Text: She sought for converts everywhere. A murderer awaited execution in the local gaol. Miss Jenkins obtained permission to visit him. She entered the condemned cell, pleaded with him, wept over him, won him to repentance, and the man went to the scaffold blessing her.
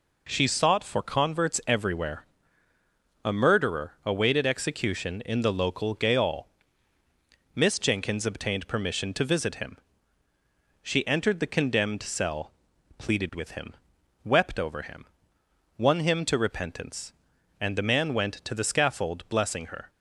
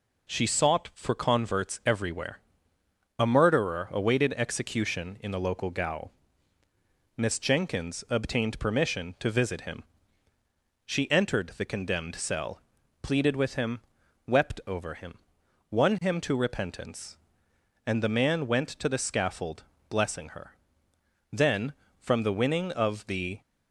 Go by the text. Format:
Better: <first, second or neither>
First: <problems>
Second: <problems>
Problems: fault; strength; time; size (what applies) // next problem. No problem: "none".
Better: first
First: none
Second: pauses between "scaffold" and "blessing"; slight; at 19.6 s; 0.24 s long // goes on to say "Then from the winning of the"; strong; from 21.3 s on; 2.0 s long